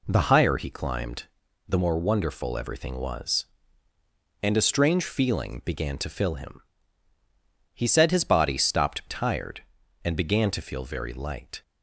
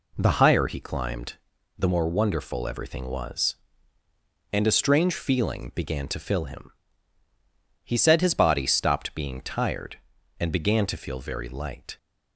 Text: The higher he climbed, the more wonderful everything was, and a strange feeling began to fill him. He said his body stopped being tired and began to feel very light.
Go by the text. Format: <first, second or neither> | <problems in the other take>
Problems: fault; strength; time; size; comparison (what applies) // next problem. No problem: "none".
second | skips "being"; at 9.0 s